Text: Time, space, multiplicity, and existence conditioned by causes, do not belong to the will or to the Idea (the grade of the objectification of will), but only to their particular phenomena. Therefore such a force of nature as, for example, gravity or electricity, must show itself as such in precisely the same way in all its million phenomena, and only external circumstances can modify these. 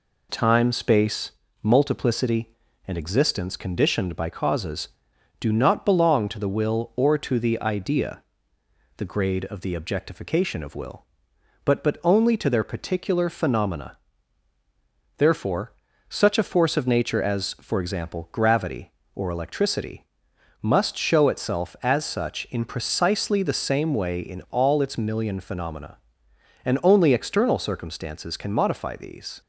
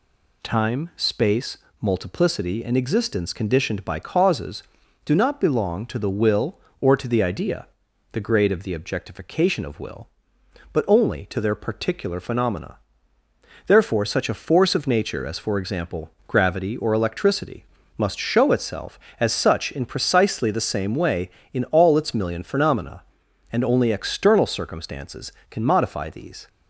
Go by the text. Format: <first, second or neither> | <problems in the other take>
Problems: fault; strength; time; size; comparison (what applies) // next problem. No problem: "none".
second | says "but" twice; at 11.8 s // pauses between "Therefore" and "such"; slight; at 15.7 s; 0.36 s long